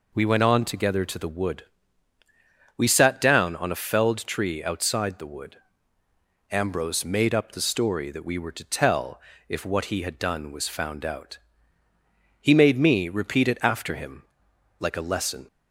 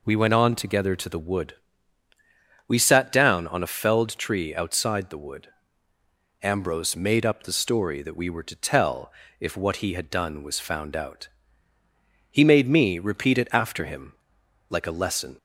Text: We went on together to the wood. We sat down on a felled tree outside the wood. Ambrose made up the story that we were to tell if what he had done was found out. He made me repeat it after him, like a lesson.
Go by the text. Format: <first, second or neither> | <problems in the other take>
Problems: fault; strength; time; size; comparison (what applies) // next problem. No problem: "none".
neither | pauses between "tell" and "if"; slight; the same in both